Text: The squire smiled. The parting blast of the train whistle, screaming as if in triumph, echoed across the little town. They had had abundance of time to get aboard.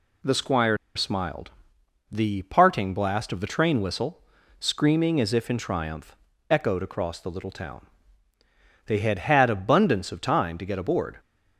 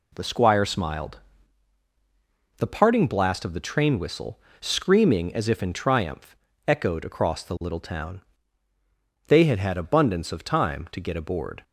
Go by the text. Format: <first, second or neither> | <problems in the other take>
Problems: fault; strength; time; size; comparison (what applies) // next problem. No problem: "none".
second | pauses between "squire" and "smiled"; slight; at 0.7 s; 0.19 s long